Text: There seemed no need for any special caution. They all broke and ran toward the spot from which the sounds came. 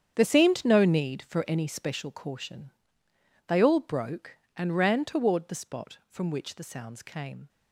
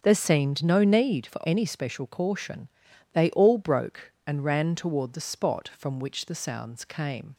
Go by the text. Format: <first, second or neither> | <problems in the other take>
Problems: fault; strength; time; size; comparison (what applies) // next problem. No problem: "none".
second | gets quieter; strong; throughout; 13.5 dB // starts louder than the rest; strong; until 1.1 s; 8.5 dB; also in the second